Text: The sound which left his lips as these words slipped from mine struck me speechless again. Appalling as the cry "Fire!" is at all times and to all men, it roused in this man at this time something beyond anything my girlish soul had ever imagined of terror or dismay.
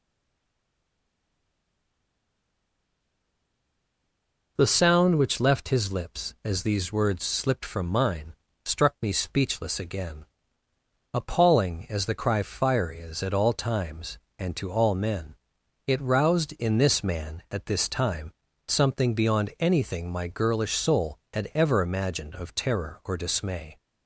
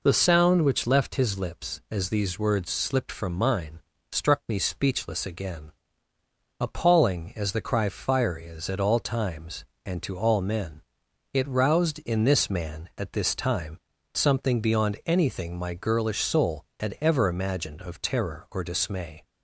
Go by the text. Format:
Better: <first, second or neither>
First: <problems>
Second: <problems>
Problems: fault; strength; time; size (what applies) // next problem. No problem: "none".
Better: second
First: stays silent before the first word; strong; until 4.5 s; 4.5 s long // pauses between "mine" and "struck"; slight; at 8.3 s; 0.32 s long // pauses between "time" and "something"; slight; at 18.3 s; 0.34 s long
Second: pauses between "mine" and "struck"; slight; at 3.7 s; 0.32 s long // pauses between "time" and "something"; slight; at 13.7 s; 0.34 s long